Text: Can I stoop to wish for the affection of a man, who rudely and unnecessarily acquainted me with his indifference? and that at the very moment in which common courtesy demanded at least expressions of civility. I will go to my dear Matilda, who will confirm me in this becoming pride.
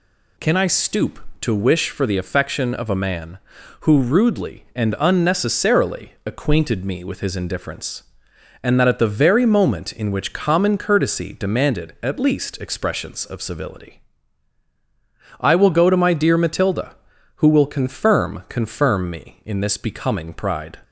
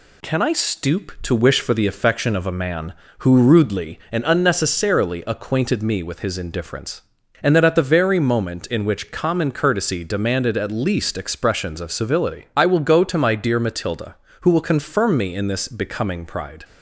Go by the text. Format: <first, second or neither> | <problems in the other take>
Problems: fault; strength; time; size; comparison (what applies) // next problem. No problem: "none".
second | says "confirm" twice; at 18.4 s